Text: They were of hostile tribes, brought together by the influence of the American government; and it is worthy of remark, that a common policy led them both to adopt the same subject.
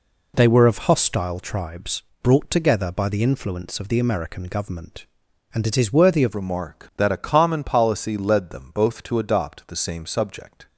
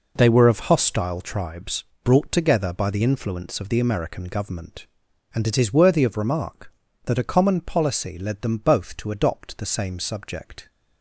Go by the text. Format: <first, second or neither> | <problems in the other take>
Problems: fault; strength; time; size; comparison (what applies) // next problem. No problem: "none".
second | changes voice at "remark"; from 6.3 s on; 4.3 s long